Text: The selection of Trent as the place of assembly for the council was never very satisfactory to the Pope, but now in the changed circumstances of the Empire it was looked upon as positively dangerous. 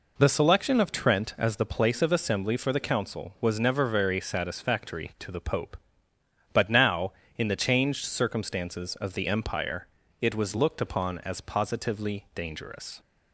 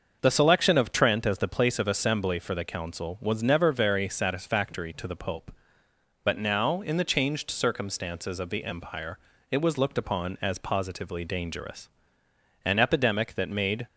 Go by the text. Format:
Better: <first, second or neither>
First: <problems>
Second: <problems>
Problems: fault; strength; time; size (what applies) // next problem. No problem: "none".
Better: first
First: pauses between "Empire" and "it"; slight; at 9.8 s; 0.34 s long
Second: starts louder than the rest; until 1.2 s; 6.5 dB // pauses between "Empire" and "it"; slight; at 9.1 s; 0.32 s long // goes on to say "An epidemic that made"; noticeable; from 12.6 s on; 1.2 s long